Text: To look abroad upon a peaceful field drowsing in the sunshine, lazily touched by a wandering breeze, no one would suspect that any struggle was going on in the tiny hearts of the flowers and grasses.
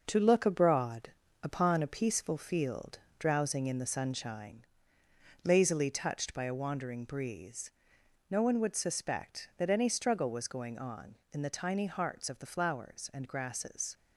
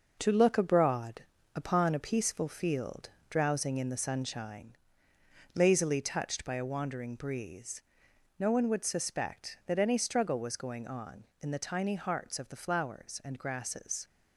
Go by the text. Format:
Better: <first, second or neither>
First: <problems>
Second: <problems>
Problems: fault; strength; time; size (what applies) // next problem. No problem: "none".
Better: neither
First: starts louder than the rest; noticeable; until 1.0 s; 6 dB // pauses between "abroad" and "upon"; slight; at 1.1 s; 0.30 s long // pauses between "field" and "drowsing"; slight; at 2.9 s; 0.20 s long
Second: starts louder than the rest; noticeable; until 1.2 s; 6 dB // pauses between "abroad" and "upon"; slight; at 1.2 s; 0.30 s long // pauses between "field" and "drowsing"; slight; at 3.0 s; 0.20 s long